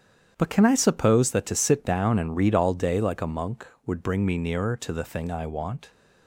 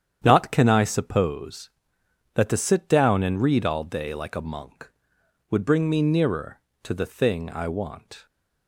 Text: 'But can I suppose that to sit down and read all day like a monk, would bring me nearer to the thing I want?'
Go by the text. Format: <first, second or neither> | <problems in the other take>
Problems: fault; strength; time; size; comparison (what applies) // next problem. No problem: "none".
first | starts louder than the rest; strong; until 1.2 s; 9 dB; strong in the first // says "Not" for "But"; at 0.2 s